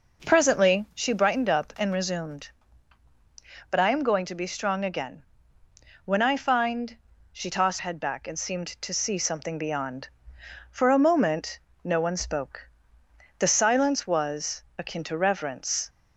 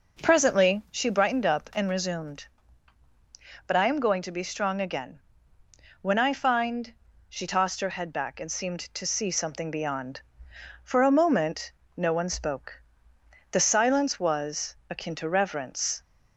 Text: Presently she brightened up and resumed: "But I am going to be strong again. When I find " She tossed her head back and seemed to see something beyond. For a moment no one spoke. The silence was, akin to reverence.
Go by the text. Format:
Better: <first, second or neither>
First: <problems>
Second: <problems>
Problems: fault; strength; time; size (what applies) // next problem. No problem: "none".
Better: second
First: skips "her"; at 7.7 s // pauses between "moment" and "no"; slight; at 11.5 s; 0.26 s long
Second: pauses between "moment" and "no"; slight; at 11.6 s; 0.26 s long